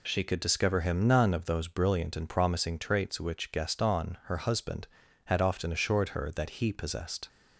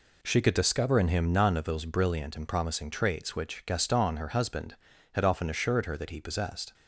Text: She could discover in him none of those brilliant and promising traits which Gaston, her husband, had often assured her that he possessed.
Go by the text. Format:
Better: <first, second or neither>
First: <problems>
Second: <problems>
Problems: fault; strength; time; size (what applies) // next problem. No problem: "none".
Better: second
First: skips "in"; at 0.8 s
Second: none